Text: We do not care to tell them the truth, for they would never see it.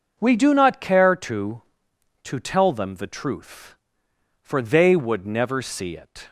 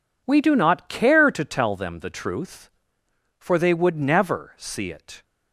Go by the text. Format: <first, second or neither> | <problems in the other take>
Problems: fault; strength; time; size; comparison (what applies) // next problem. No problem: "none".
second | says "to" twice; at 2.2 s